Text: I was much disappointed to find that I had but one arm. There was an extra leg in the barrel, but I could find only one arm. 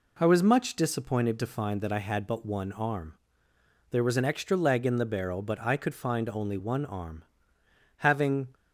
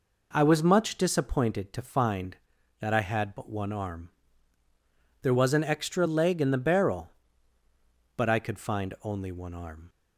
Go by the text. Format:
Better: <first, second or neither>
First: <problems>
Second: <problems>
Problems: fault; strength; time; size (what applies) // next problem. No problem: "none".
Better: second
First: goes on to say "Having"; from 7.9 s on; 0.56 s long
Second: none